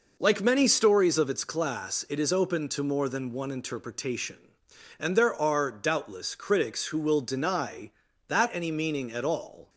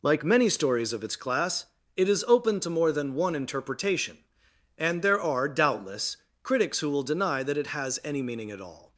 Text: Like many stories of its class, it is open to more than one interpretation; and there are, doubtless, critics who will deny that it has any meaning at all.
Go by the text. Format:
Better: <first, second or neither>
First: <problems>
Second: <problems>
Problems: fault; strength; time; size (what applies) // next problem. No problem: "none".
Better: second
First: skips "it has"; at 8.5 s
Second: none